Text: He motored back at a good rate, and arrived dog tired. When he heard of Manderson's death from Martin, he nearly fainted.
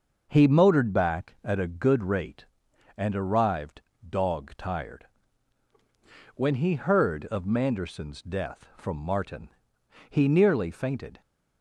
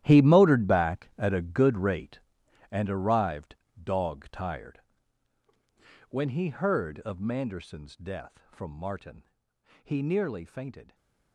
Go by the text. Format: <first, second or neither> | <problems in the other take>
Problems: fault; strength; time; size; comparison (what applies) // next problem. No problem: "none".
first | gets quieter; strong; throughout; 15.5 dB // starts louder than the rest; strong; until 1.0 s; 12.5 dB; noticeable in the first // pauses between "arrived" and "dog"; slight; at 3.5 s; 0.26 s long; slight in the first // stays silent after the last word; slight; from 10.8 s on; 0.5 s long